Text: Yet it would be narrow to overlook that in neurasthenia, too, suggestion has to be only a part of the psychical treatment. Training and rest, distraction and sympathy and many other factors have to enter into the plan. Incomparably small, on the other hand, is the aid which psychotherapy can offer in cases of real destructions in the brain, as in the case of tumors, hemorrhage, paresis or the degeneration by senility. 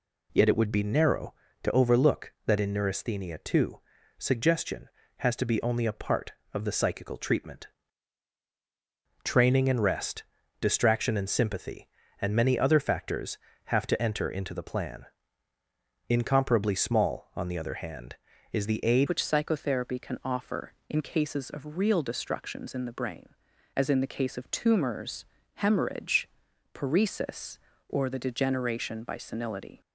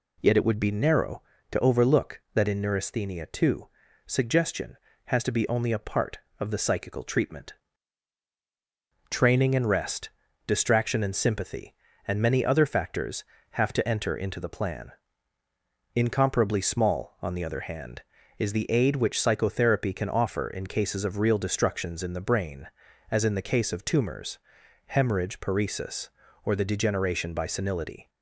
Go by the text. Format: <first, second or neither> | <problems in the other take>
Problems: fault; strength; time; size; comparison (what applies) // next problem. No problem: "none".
second | changes voice at "which"; from 19.0 s on; 10.8 s long